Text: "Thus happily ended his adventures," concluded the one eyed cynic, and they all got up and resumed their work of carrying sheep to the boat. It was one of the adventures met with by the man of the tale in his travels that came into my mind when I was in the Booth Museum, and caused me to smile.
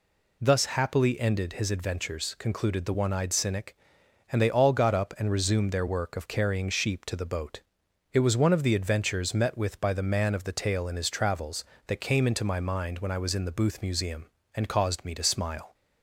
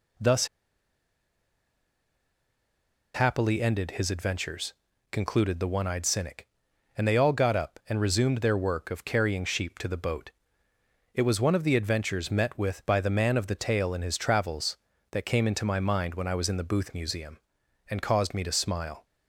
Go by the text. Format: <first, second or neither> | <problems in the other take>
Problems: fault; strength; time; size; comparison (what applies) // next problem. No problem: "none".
first | pauses between "Thus" and "happily"; strong; at 0.4 s; 2.6 s long